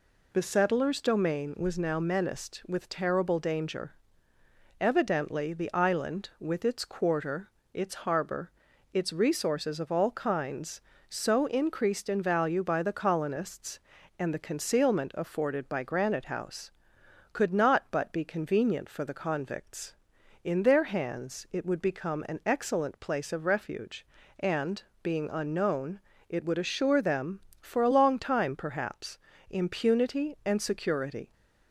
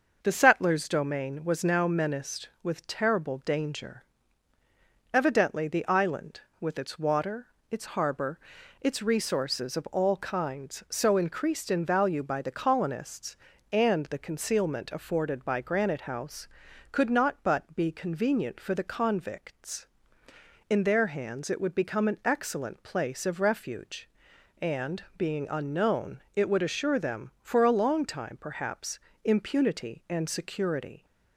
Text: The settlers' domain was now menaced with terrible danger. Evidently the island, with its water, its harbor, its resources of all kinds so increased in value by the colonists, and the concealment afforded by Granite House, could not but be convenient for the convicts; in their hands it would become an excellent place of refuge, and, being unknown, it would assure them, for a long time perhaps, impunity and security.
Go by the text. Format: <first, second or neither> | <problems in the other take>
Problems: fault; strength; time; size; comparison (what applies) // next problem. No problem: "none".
second | says "quarter" for "water"; at 6.8 s